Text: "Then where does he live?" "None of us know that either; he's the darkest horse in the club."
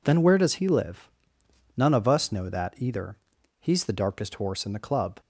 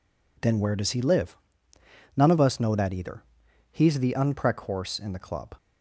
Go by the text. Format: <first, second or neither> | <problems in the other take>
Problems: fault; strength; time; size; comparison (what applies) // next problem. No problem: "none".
first | says "unprec" for "darkest"; at 4.1 s